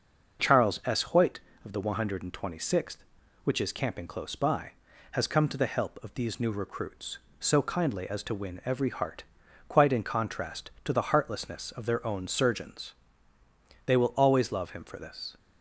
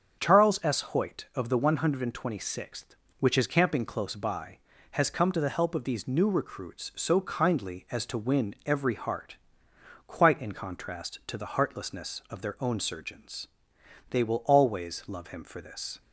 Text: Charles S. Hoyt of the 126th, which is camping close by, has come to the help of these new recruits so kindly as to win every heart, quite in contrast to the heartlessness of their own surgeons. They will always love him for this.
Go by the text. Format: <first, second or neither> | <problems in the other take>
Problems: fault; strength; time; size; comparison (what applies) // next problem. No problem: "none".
neither | starts louder than the rest; the same in both